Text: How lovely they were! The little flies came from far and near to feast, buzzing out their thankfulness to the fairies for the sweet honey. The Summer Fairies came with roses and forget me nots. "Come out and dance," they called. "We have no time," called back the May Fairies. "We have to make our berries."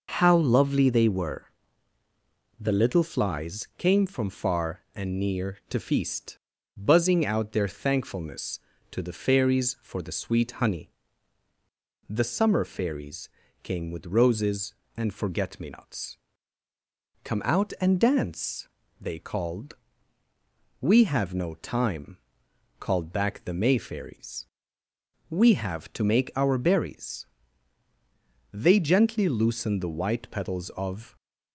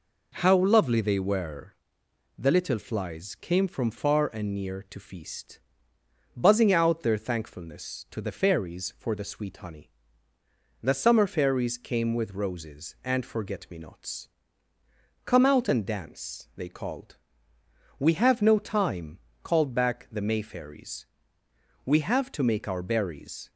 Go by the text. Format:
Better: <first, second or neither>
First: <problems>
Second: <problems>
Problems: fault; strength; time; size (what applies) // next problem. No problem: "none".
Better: second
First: pauses between "Fairies" and "came"; slight; at 13.2 s; 0.34 s long // goes on to say "They gently loosened the white petals of"; strong; from 28.5 s on; 2.6 s long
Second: none